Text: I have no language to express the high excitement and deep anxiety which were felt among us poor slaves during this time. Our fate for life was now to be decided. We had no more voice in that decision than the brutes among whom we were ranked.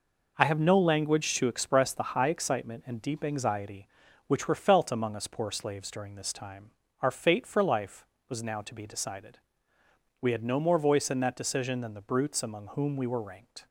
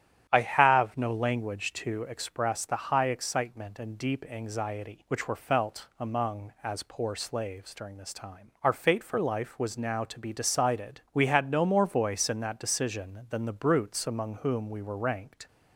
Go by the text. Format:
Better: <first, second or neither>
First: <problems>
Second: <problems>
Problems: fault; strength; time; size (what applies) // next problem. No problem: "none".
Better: first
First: none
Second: starts louder than the rest; strong; until 1.3 s; 10.5 dB // says "as" for "us"; at 6.6 s